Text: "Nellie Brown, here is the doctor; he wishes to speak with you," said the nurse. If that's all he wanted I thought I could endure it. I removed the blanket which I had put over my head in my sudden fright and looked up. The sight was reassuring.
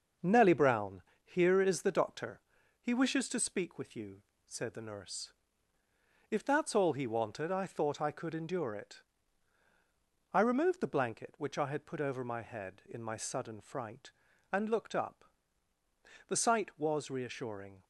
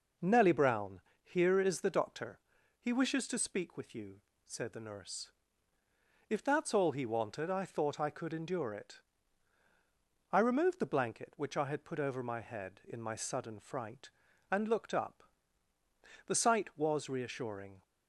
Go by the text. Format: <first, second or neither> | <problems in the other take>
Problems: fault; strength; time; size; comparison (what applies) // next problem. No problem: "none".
second | gets quieter; noticeable; throughout; 5.5 dB